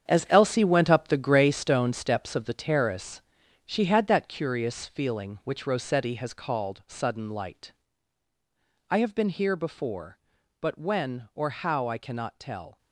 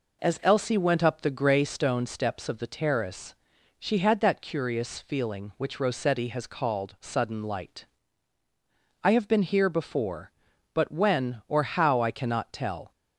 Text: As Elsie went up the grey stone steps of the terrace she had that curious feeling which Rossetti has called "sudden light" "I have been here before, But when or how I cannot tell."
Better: second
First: gets quieter; strong; throughout; 11.5 dB // pauses between "terrace" and "she"; noticeable; at 3.2 s; 0.46 s long // pauses between "light" and "I"; at 7.7 s; 1.1 s long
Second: pauses between "terrace" and "she"; noticeable; at 3.3 s; 0.46 s long // pauses between "light" and "I"; at 7.8 s; 1.1 s long

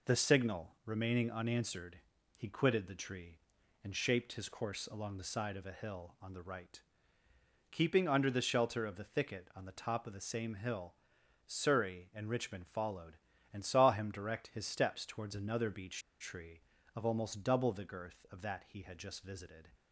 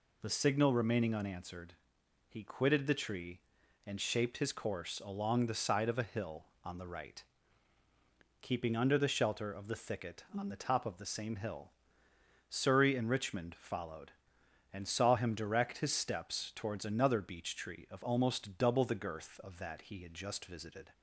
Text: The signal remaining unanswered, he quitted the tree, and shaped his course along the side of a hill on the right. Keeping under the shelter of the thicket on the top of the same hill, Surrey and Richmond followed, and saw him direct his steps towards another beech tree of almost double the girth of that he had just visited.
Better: second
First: pauses between "beech" and "tree"; slight; at 16.0 s; 0.19 s long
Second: none

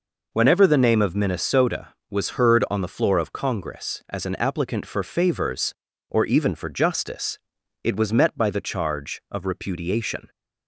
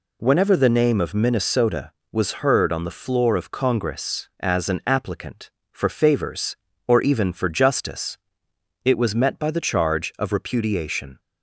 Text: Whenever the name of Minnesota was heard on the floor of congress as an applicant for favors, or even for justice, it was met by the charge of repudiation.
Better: neither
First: none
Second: none

